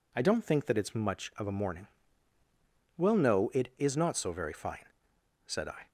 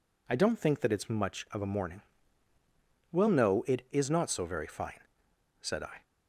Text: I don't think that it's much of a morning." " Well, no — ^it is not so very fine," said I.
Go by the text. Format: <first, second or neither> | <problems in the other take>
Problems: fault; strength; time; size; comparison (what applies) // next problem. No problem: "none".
neither | none